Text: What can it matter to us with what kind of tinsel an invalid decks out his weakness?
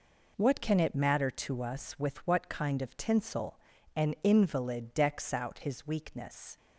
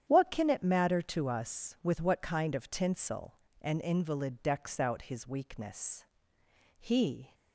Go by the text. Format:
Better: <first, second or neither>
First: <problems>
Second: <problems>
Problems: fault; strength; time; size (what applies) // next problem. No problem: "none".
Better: first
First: pauses between "tinsel" and "an"; slight; at 3.5 s; 0.36 s long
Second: starts louder than the rest; strong; until 1.0 s; 9.5 dB // pauses between "tinsel" and "an"; slight; at 3.3 s; 0.26 s long // goes on to say "He"; from 6.7 s on; 0.54 s long